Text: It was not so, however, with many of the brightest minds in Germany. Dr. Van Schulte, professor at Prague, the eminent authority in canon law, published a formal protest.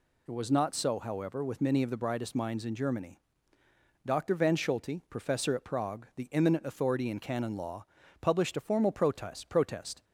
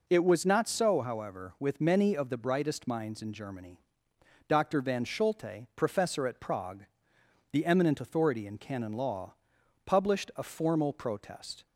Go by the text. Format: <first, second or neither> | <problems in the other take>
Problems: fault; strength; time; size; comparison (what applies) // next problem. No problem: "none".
second | says "protest" twice; at 9.4 s